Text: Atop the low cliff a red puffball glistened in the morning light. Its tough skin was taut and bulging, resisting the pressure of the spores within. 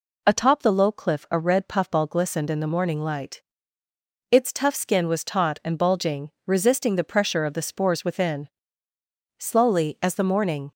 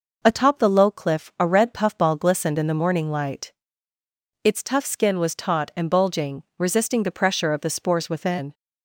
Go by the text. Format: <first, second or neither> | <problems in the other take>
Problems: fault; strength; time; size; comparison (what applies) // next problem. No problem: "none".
second | goes on to say "Slowly as the morning"; from 9.3 s on; 1.3 s long